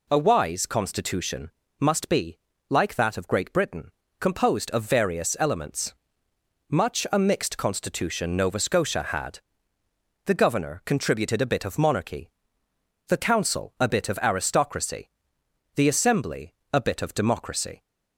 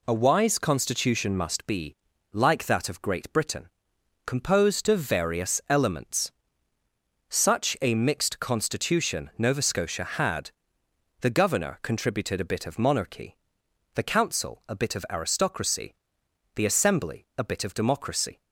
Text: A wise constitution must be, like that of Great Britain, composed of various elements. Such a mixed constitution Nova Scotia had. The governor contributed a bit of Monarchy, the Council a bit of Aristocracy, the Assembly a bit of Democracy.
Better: second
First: pauses between "constitution" and "must"; slight; at 1.4 s; 0.32 s long // says "Much" for "Such"; at 6.6 s // pauses between "Assembly" and "a"; slight; at 16.5 s; 0.18 s long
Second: none

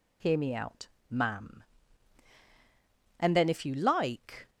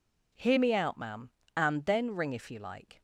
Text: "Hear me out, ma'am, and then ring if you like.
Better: second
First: skips "ring"; at 3.4 s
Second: none

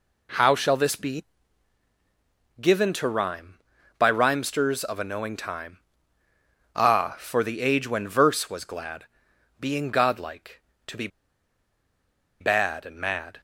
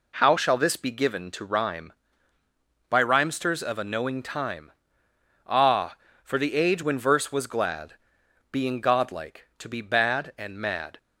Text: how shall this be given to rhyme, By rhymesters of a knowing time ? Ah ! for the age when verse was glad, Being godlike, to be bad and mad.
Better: second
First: pauses between "be" and "given"; strong; at 1.2 s; 1.3 s long // pauses between "be" and "bad"; strong; at 11.0 s; 1.3 s long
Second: none

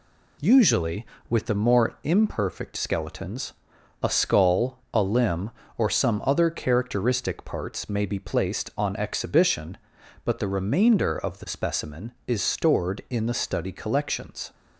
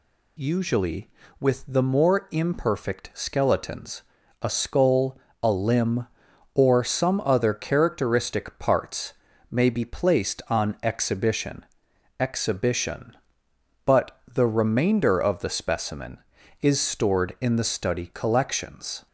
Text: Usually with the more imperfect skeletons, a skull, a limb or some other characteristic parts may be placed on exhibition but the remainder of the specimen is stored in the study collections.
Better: first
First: none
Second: pauses between "parts" and "may"; slight; at 9.1 s; 0.36 s long // says "exhibition" twice; at 12.1 s

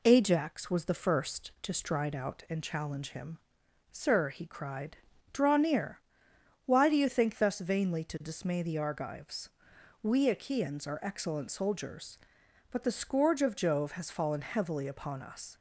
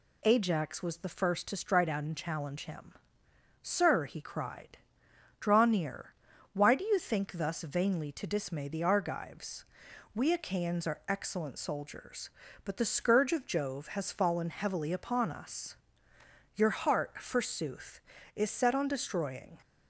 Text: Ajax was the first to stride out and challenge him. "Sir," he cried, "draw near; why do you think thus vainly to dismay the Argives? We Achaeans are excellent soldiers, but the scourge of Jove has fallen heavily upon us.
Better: first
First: none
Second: goes on to say "Your heart forsooth is set on destroying"; strong; from 16.5 s on; 3.0 s long

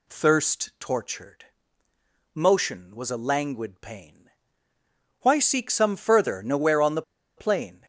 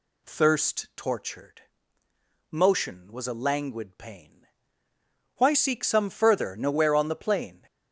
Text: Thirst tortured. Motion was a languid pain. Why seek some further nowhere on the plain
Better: second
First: pauses between "the" and "plain"; slight; at 7.0 s; 0.34 s long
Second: none

